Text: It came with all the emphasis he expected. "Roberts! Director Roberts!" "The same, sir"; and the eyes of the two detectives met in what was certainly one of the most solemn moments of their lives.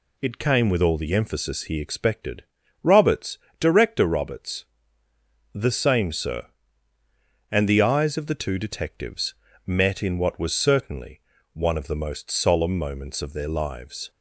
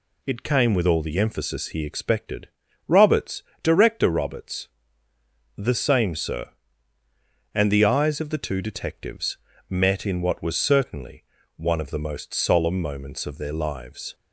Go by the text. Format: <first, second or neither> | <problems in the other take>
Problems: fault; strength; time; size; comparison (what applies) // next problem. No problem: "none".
neither | pauses between "detectives" and "met"; slight; the same in both // pauses between "certainly" and "one"; slight; the same in both